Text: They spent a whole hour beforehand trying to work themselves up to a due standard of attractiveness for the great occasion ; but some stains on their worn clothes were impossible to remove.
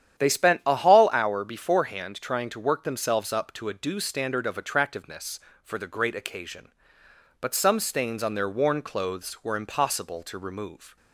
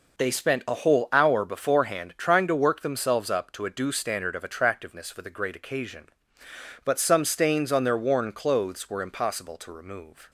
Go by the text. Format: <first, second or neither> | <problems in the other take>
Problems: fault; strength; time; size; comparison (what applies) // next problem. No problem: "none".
second | starts louder than the rest; strong; until 1.2 s; 10 dB // says "hall" for "whole"; at 0.7 s